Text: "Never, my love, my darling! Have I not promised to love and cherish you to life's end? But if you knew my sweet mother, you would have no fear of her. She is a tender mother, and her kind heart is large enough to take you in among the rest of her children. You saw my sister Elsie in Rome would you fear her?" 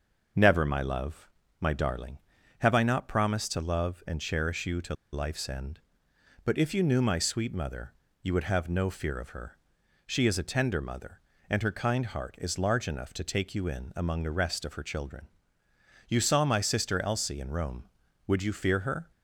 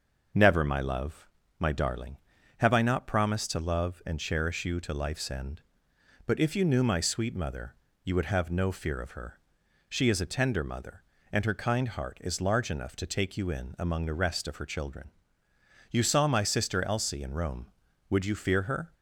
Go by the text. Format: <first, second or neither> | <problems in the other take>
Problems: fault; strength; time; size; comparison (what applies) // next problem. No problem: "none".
second | starts louder than the rest; noticeable; until 1.6 s; 6 dB; noticeable in the second // pauses between "to" and "life's"; slight; at 4.9 s; 0.17 s long